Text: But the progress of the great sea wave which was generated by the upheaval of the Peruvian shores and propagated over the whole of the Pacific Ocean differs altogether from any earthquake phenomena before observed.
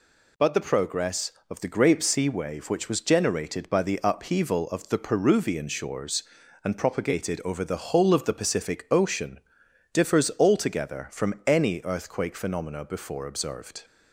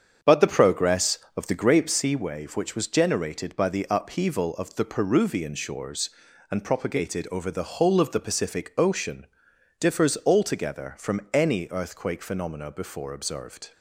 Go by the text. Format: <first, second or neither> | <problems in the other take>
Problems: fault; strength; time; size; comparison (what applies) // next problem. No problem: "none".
first | starts louder than the rest; strong; until 1.7 s; 7.5 dB // pauses between "Ocean" and "differs"; noticeable; at 9.2 s; 0.54 s long; noticeable in the first